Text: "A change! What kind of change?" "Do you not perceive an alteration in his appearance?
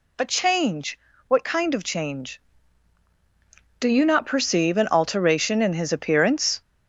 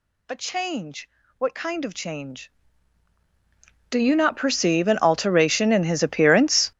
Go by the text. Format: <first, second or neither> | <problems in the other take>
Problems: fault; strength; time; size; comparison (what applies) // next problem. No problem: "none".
first | gets louder; strong; throughout; 16 dB